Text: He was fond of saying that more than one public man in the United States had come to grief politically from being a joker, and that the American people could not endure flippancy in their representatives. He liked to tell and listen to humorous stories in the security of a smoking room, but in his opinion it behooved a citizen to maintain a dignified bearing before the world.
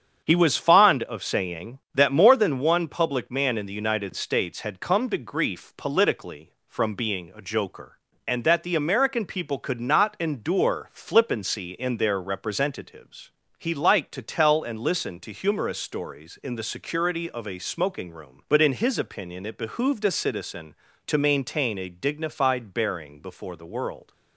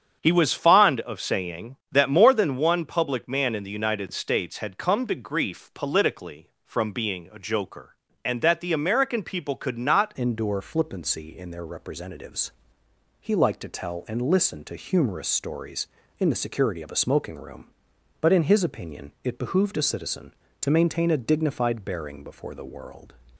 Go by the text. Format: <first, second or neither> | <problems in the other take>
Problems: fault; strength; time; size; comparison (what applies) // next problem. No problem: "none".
first | starts louder than the rest; strong; until 1.2 s; 8 dB; strong in the first // changes voice at "endure"; from 10.1 s on; 13.0 s long